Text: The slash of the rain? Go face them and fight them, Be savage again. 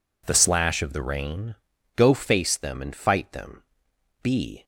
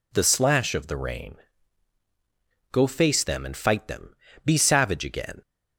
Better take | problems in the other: second | stops before "savage again"; at 4.6 s

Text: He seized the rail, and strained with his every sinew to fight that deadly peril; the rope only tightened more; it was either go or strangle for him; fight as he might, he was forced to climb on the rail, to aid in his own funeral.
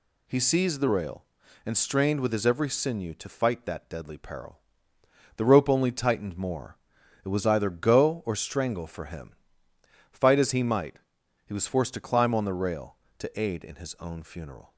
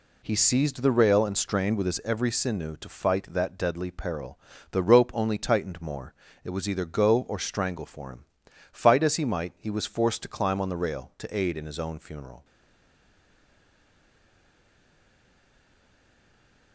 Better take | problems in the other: first | stays silent after the last word; strong; from 12.4 s on; 4.3 s long

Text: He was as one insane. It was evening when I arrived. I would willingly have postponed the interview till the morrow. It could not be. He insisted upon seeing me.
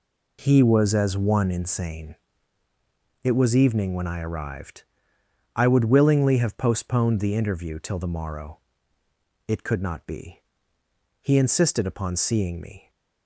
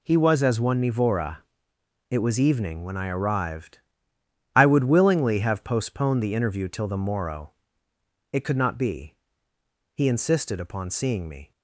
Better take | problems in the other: first | says "nivora" for "insane"; at 0.8 s

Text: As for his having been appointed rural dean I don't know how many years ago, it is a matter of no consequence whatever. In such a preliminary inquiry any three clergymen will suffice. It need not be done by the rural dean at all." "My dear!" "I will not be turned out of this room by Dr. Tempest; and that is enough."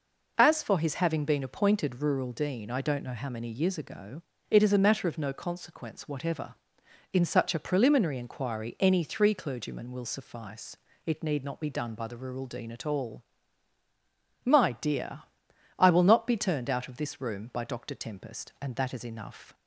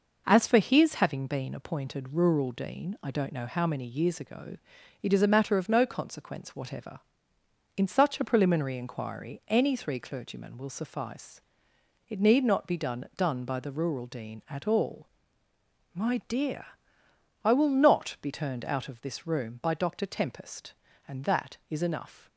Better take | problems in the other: first | says "done" twice; at 13.1 s

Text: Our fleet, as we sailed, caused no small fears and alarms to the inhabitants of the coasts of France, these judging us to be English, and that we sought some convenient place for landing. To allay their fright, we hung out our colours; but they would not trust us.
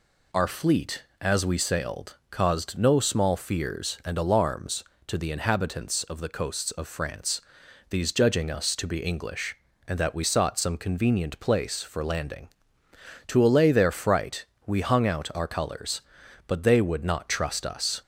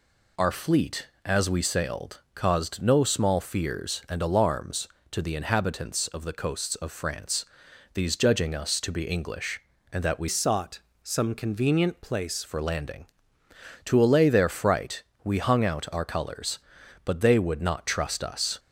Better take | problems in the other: first | changes voice from "sought" to "place"; from 10.2 to 12.4 s; 2.2 s long // pauses between "sought" and "some"; slight; at 10.7 s; 0.24 s long

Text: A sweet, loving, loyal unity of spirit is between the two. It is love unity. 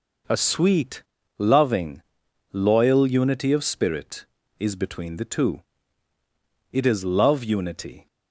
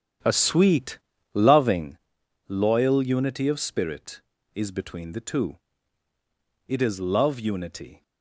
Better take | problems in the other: first | starts louder than the rest; strong; until 2.0 s; 9 dB

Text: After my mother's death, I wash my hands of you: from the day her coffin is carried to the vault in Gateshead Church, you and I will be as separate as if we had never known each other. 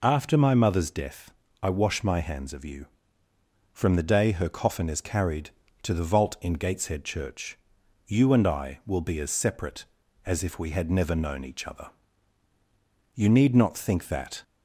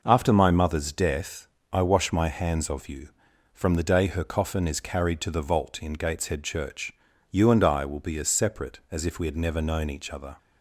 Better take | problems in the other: second | goes on to say "You need not think that"; noticeable; from 13.1 s on; 1.2 s long

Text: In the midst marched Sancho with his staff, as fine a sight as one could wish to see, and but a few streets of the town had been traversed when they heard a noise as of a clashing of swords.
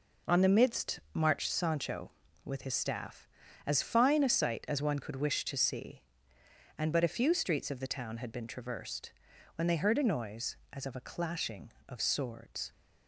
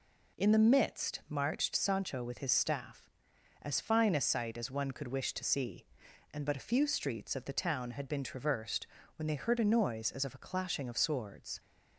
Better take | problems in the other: second | says "On" for "In"; at 0.2 s // pauses between "midst" and "marched"; slight; at 0.9 s; 0.16 s long // pauses between "traversed" and "when"; at 9.1 s; 0.44 s long; slight in the second

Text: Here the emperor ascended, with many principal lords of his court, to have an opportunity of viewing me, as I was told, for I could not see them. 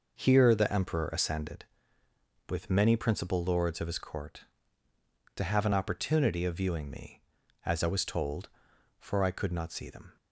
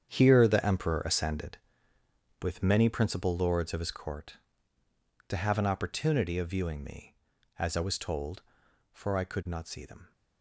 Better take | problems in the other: first | gets quieter; strong; throughout; 13 dB

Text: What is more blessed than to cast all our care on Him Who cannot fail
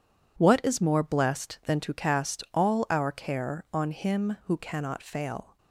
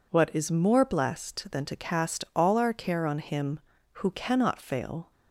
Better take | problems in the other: neither | none

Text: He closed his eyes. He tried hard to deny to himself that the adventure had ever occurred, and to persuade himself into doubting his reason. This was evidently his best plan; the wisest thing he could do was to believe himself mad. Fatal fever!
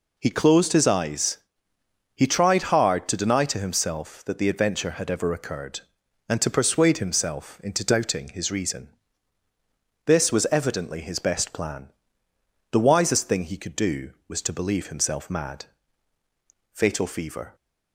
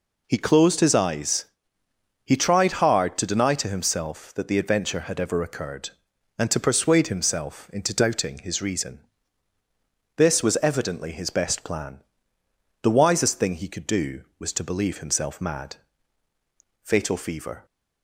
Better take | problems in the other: neither | none

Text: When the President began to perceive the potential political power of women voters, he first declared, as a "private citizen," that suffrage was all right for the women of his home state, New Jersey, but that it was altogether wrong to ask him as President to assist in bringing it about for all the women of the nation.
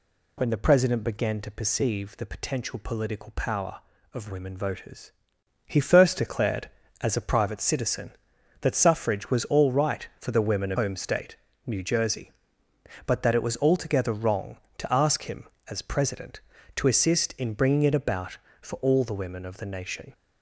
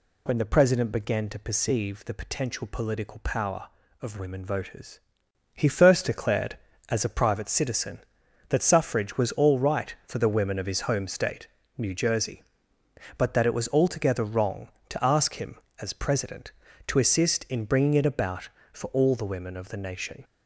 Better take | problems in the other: second | skips "his"; at 10.7 s

